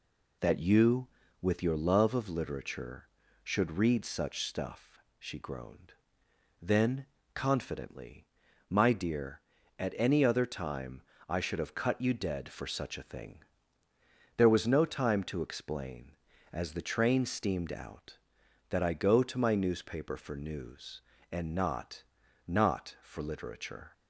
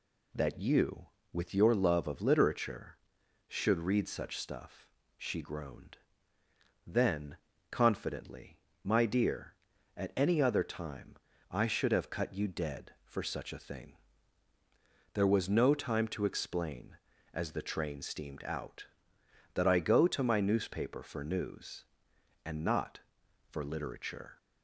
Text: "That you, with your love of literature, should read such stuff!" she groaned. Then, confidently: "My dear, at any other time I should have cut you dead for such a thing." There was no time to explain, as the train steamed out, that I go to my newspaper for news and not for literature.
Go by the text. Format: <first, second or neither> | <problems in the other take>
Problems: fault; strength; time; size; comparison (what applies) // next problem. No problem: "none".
second | pauses between "time" and "I"; slight; at 11.0 s; 0.26 s long; slight in the second // says "not" twice; at 22.4 s